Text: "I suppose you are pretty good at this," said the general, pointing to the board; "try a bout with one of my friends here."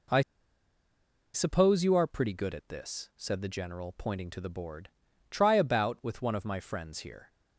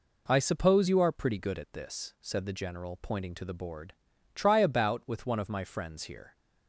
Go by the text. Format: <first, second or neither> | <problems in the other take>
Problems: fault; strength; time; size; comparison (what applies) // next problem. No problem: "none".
second | pauses between "I" and "suppose"; at 0.2 s; 1.1 s long